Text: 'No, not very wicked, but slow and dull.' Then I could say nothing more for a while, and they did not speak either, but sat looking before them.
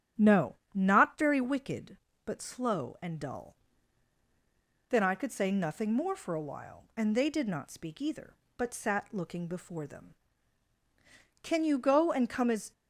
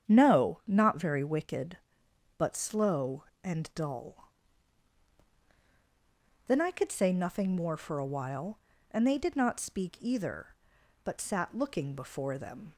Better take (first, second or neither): second